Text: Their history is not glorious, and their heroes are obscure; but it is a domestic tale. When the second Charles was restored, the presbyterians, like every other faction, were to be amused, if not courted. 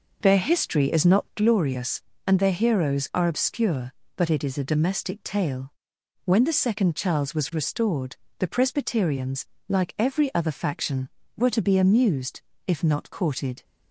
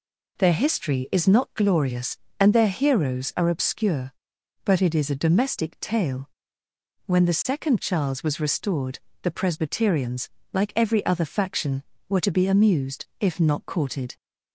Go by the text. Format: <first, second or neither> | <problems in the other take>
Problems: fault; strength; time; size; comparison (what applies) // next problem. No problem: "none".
second | starts louder than the rest; noticeable; until 1.5 s; 5.5 dB